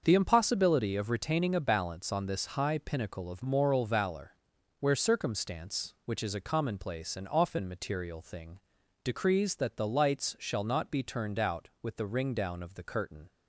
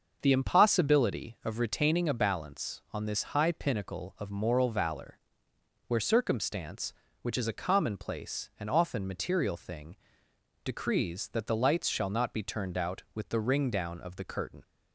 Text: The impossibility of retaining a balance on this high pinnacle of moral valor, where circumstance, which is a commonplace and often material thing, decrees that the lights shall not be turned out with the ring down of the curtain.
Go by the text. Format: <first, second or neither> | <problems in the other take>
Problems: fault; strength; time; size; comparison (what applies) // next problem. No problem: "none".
neither | starts louder than the rest; the same in both